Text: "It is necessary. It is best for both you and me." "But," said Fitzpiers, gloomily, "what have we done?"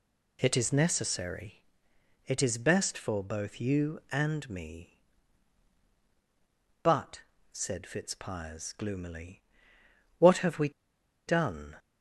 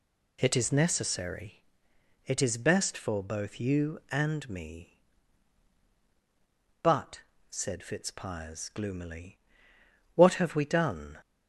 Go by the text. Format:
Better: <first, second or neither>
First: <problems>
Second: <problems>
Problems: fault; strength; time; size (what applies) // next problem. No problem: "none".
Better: second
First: pauses between "we" and "done"; noticeable; at 10.6 s; 0.57 s long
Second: none